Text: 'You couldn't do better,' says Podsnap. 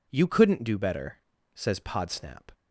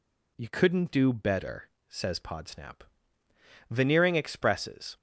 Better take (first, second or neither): first